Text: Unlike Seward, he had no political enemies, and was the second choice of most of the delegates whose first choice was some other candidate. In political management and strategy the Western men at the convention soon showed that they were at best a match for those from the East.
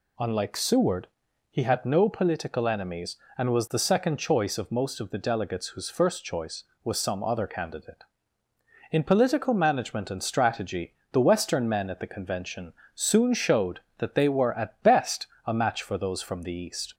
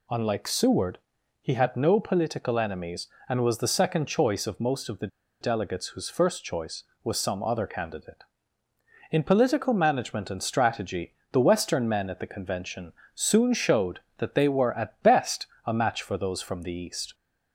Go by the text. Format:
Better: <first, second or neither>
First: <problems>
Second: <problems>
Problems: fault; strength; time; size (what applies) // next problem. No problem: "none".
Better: first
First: pauses between "strategy" and "the"; slight; at 10.9 s; 0.18 s long // pauses between "convention" and "soon"; slight; at 12.7 s; 0.22 s long // pauses between "best" and "a"; slight; at 15.2 s; 0.20 s long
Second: pauses between "the" and "delegates"; slight; at 5.0 s; 0.34 s long // pauses between "strategy" and "the"; slight; at 11.1 s; 0.18 s long // pauses between "convention" and "soon"; slight; at 12.9 s; 0.22 s long // pauses between "best" and "a"; slight; at 15.4 s; 0.20 s long